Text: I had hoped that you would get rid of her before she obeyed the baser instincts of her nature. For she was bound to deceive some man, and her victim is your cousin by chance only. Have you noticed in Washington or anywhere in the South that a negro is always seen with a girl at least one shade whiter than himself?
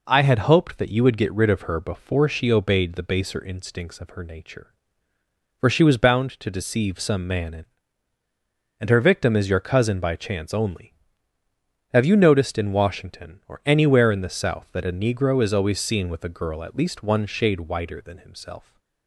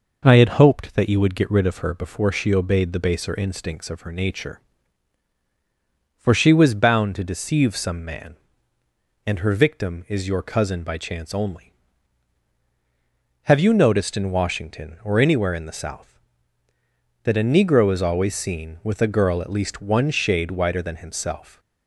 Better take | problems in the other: second | says "and" twice; at 8.7 s

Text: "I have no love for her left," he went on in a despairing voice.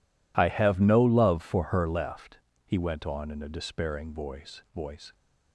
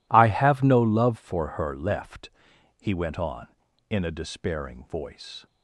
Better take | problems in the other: second | says "voice" twice; at 4.7 s

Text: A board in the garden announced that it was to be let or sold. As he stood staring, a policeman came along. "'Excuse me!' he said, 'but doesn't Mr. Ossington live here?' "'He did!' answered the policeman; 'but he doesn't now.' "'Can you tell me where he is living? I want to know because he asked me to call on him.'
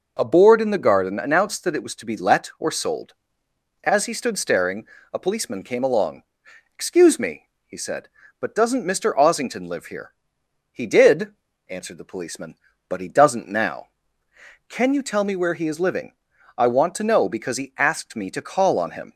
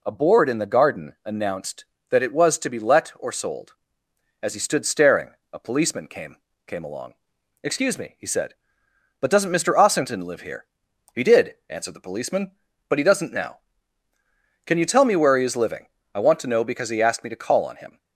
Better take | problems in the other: first | says "came" twice; at 6.6 s

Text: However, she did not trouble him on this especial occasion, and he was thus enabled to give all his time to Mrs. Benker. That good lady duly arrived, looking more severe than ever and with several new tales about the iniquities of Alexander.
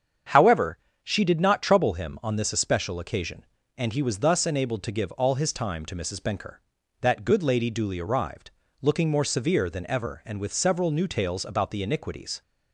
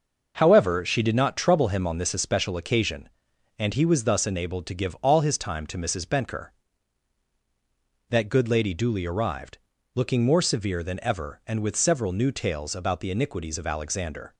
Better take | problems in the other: second | starts louder than the rest; strong; until 1.6 s; 7.5 dB; noticeable in the second // stops before "of Alexander"; at 12.4 s

